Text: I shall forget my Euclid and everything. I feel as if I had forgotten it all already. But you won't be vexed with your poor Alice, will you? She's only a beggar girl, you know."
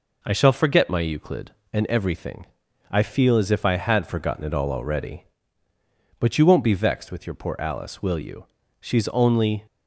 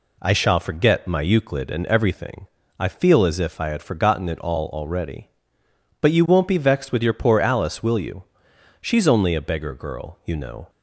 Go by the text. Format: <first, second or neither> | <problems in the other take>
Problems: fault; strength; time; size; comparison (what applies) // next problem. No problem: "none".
second | stops before "a beggar girl you know"; at 9.6 s